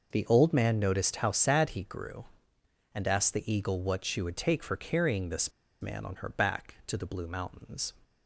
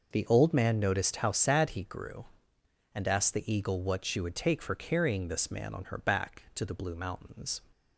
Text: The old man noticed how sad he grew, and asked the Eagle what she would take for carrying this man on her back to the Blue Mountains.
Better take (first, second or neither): second